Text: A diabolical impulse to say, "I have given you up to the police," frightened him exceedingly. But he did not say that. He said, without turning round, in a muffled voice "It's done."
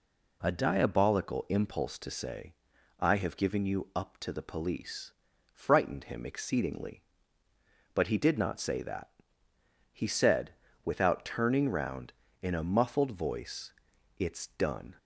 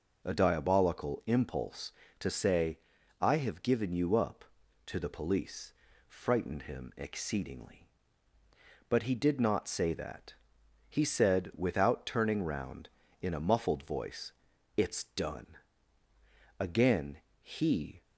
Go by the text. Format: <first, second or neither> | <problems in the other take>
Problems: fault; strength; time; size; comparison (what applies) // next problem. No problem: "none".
first | pauses between "voice" and "It's"; at 14.3 s; 0.44 s long; also in the first // goes on to say "Again he"; from 16.5 s on; 1.4 s long